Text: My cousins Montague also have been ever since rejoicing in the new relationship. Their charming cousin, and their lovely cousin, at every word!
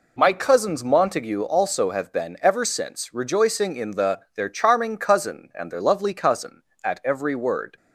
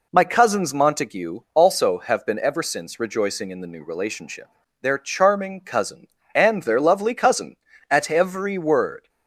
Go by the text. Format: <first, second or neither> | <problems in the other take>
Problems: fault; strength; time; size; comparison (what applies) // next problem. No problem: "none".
second | skips "new relationship"; at 4.2 s